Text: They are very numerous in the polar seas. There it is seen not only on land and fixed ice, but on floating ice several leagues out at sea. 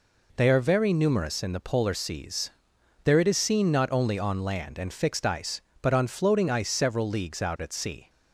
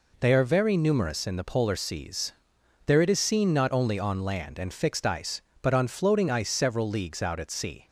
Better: neither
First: none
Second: none

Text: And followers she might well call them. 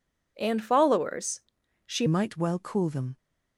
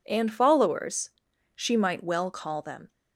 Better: second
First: pauses between "followers" and "she"; at 1.4 s; 0.44 s long // changes voice at "might"; from 2.0 s on; 1.1 s long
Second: pauses between "followers" and "she"; at 1.1 s; 0.44 s long

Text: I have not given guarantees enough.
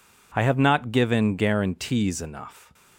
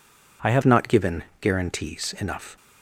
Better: first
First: none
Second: changes voice at "not"; from 0.6 s on; 1.9 s long // pauses between "given" and "guarantees"; slight; at 1.2 s; 0.20 s long

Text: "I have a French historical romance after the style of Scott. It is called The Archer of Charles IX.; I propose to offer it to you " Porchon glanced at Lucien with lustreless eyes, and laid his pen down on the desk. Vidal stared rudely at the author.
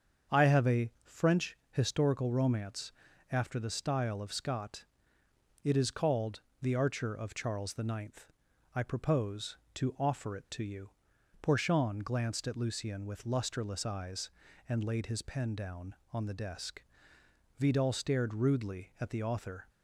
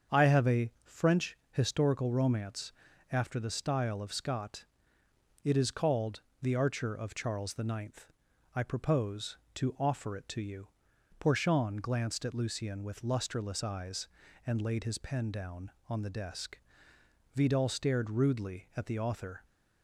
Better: neither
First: starts louder than the rest; strong; until 1.4 s; 7 dB // pauses between "romance" and "after"; at 2.9 s; 0.40 s long // pauses between "called" and "The"; slight; at 6.4 s; 0.20 s long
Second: starts louder than the rest; strong; until 1.2 s; 7 dB // pauses between "romance" and "after"; at 2.7 s; 0.40 s long // pauses between "called" and "The"; slight; at 6.2 s; 0.20 s long

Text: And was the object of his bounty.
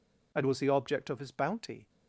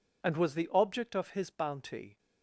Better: neither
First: none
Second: none

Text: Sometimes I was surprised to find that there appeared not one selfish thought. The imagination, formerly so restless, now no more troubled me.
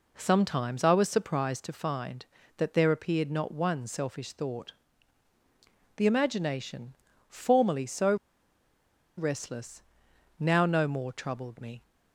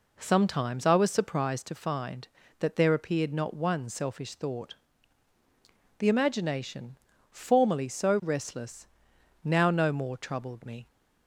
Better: second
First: pauses between "so" and "restless"; at 8.1 s; 1.0 s long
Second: none

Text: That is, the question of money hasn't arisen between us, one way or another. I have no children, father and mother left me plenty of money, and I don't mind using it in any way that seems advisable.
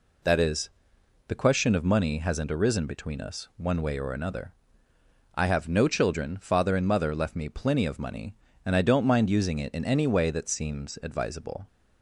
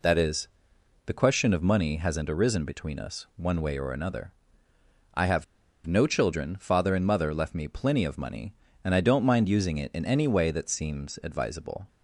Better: first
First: none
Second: pauses between "have" and "no"; at 5.4 s; 0.42 s long

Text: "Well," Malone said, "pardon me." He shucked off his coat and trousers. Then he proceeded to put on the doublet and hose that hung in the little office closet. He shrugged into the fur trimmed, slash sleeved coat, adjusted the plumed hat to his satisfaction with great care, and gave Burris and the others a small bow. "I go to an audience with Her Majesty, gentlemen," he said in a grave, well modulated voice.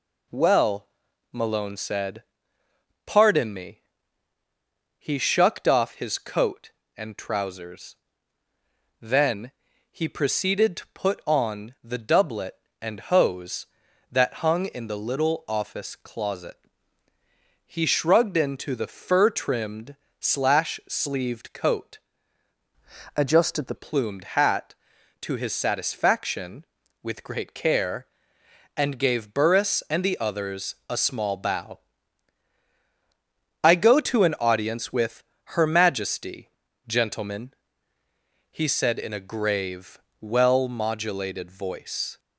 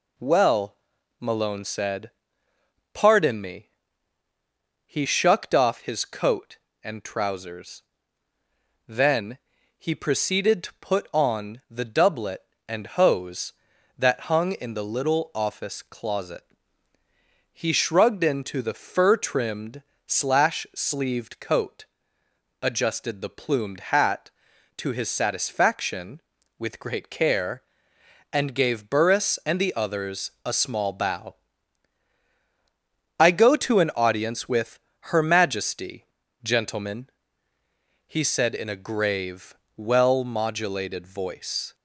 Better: second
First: pauses between "Then" and "he"; at 9.5 s; 0.38 s long // changes voice from "adjusted" to "the"; from 23.1 to 23.7 s; 0.6 s long // pauses between "with" and "Her"; slight; at 35.2 s; 0.32 s long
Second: pauses between "Then" and "he"; at 9.3 s; 0.38 s long // pauses between "with" and "Her"; slight; at 34.7 s; 0.32 s long

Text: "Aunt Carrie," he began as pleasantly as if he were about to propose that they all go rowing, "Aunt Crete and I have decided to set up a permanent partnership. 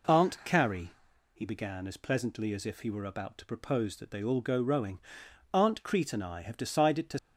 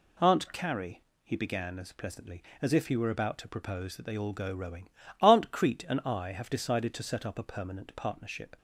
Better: second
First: stops before "set up a permanent partnership"; at 7.1 s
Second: none

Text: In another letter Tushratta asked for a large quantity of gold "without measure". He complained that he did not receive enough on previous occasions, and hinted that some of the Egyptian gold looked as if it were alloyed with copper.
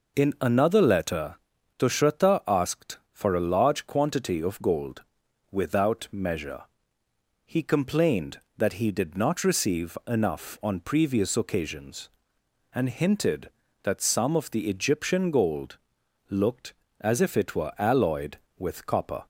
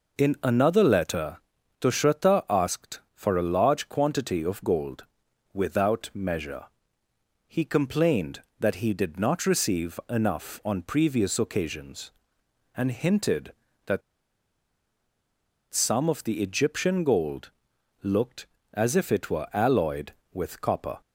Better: first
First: pauses between "letter" and "Tushratta"; at 1.3 s; 0.42 s long // pauses between "gold" and "without"; noticeable; at 5.0 s; 0.48 s long // pauses between "gold" and "looked"; noticeable; at 15.7 s; 0.50 s long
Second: pauses between "letter" and "Tushratta"; at 1.3 s; 0.42 s long // pauses between "gold" and "without"; noticeable; at 5.0 s; 0.48 s long // pauses between "that" and "some"; strong; at 14.0 s; 1.7 s long // pauses between "gold" and "looked"; noticeable; at 17.5 s; 0.50 s long

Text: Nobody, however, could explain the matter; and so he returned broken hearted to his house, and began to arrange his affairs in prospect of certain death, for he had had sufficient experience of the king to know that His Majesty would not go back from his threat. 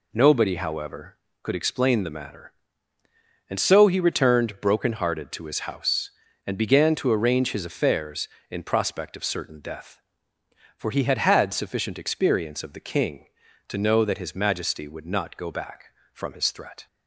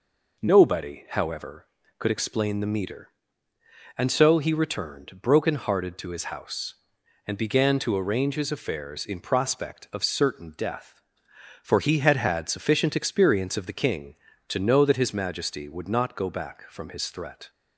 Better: first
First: none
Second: says "meter" for "matter"; at 2.6 s

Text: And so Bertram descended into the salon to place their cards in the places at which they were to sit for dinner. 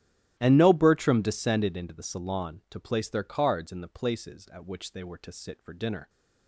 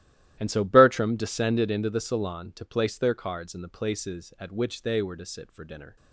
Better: second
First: starts louder than the rest; strong; until 1.4 s; 14 dB // says "no" for "so"; at 0.5 s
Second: starts louder than the rest; strong; until 1.4 s; 14 dB

